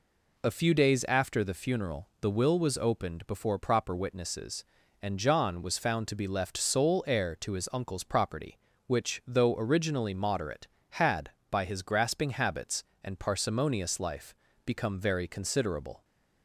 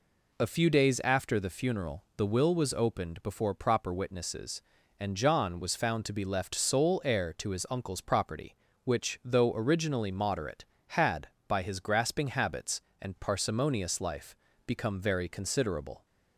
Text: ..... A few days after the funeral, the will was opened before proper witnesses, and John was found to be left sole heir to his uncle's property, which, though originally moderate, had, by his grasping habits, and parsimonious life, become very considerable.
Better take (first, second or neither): neither